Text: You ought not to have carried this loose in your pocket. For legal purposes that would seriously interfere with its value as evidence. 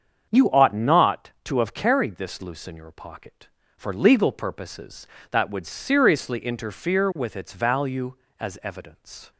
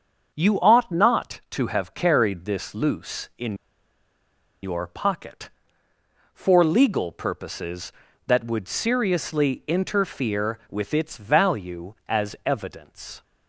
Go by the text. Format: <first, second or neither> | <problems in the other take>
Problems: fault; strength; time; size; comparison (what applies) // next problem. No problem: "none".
first | starts louder than the rest; until 1.3 s; 7 dB; strong in the first // pauses between "in" and "your"; at 3.5 s; 1.0 s long